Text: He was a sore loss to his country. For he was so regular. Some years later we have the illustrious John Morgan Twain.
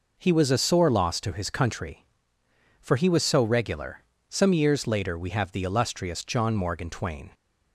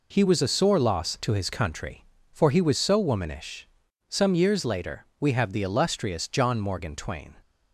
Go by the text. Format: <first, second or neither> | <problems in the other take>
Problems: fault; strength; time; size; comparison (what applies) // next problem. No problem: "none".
first | says "womanish" for "regular"; at 2.9 s // pauses between "later" and "we"; slight; at 5.0 s; 0.16 s long